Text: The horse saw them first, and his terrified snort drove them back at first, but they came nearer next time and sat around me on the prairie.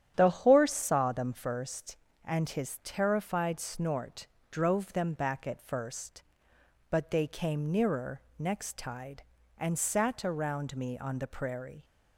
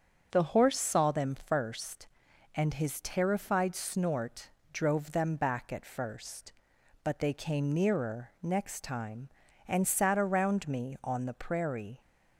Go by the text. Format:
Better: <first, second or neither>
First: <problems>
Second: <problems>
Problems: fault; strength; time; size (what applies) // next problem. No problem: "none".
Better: second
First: starts louder than the rest; strong; until 1.1 s; 10 dB // pauses between "snort" and "drove"; slight; at 4.2 s; 0.24 s long // pauses between "nearer" and "next"; slight; at 8.2 s; 0.18 s long // says "tide" for "time"; at 8.7 s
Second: starts louder than the rest; strong; until 1.3 s; 7 dB // pauses between "snort" and "drove"; slight; at 4.5 s; 0.22 s long